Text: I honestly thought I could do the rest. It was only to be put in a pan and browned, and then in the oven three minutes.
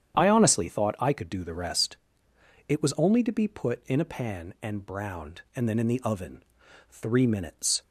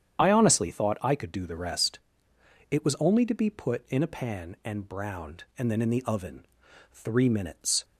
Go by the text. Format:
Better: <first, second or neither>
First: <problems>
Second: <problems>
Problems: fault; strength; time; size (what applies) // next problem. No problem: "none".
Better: first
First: starts louder than the rest; strong; until 1.1 s; 9.5 dB // pauses between "oven" and "three"; noticeable; at 6.4 s; 0.48 s long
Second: loses the start of "I"; at 0.1 s; 25 ms // starts louder than the rest; strong; until 1.2 s; 9 dB // pauses between "oven" and "three"; noticeable; at 6.4 s; 0.48 s long